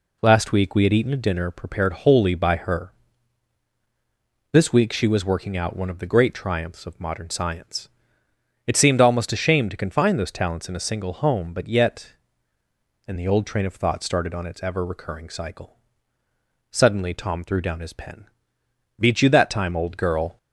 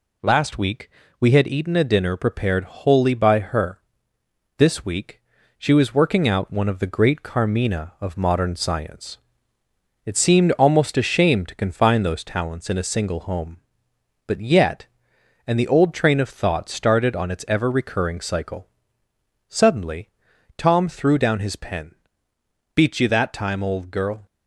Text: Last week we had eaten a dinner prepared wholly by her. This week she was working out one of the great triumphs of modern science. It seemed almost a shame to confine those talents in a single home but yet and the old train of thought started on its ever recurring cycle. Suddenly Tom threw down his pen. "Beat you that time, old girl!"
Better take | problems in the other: first | pauses between "week" and "we"; slight; at 0.8 s; 0.30 s long // pauses between "week" and "she"; at 5.1 s; 0.38 s long // says "carmina" for "triumphs"; at 7.2 s // pauses between "Suddenly" and "Tom"; noticeable; at 20.0 s; 0.48 s long

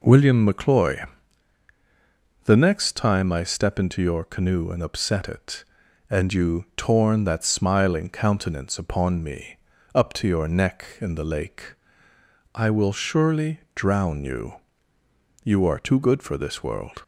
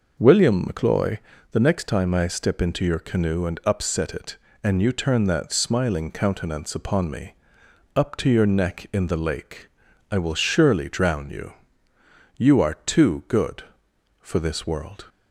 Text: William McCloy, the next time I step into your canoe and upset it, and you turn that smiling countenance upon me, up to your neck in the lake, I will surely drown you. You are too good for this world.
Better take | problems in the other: second | says "torn" for "turn"; at 6.7 s

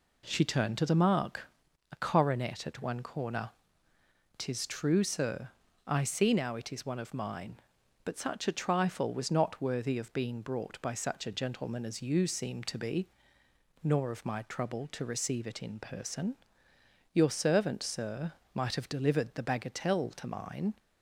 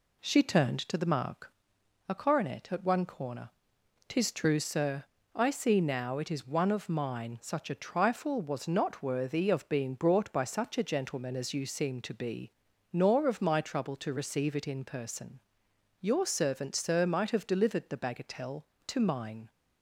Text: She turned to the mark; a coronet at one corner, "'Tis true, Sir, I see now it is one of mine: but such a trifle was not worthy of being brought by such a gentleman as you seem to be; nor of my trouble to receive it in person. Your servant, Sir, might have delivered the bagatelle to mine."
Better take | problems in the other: first | skips "but"; at 7.3 s

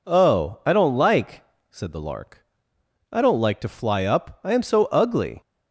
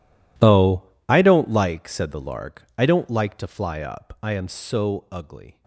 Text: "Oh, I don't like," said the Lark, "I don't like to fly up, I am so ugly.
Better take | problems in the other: first | gets quieter; strong; throughout; 21.5 dB

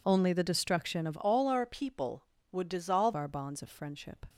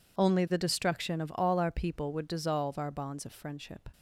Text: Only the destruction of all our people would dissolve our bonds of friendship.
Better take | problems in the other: second | changes voice from "all" to "dissolve"; from 1.2 to 3.1 s; 1.9 s long

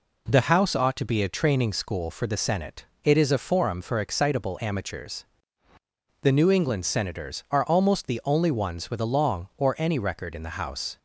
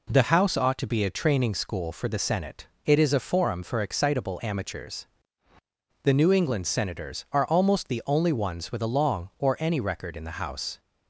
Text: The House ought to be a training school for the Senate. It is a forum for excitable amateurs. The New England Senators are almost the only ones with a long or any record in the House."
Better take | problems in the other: neither | none

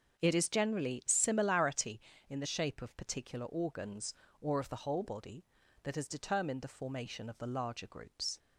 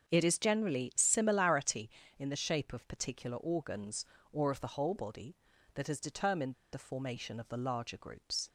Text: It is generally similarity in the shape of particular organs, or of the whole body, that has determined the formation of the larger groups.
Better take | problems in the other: first | starts louder than the rest; until 1.1 s; 7 dB; also in the first // pauses between "determined" and "the"; slight; at 6.5 s; 0.18 s long

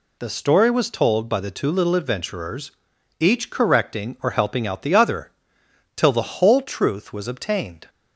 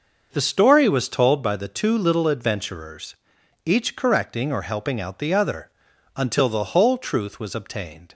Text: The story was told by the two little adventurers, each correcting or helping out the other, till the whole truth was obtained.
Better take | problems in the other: first | starts louder than the rest; noticeable; until 1.3 s; 6 dB // says "until" for "till"; at 6.1 s

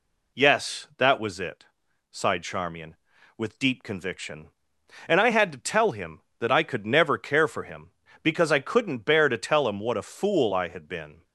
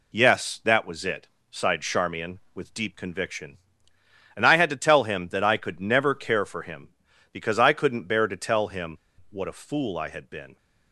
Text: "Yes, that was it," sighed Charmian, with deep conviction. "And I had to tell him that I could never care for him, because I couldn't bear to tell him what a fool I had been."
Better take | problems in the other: first | pauses between "him" and "what"; slight; at 8.9 s; 0.31 s long

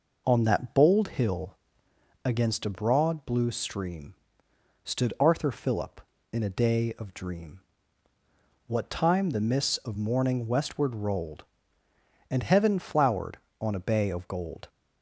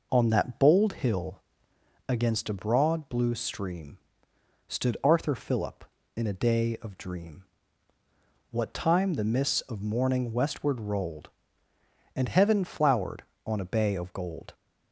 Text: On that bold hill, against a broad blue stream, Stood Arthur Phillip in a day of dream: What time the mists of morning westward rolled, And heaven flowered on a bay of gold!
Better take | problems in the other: neither | none

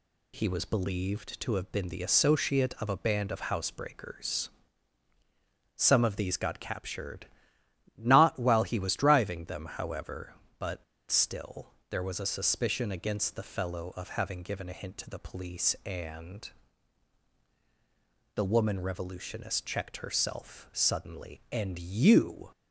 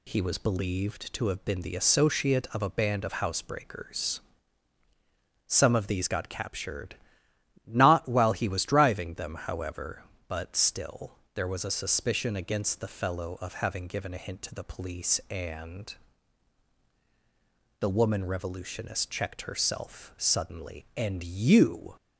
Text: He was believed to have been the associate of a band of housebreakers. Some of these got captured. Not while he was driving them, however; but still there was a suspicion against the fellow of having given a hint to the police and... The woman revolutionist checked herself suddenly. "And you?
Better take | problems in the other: second | pauses between "but" and "still"; slight; at 10.8 s; 0.27 s long // pauses between "still" and "there"; slight; at 11.7 s; 0.20 s long; slight in the second

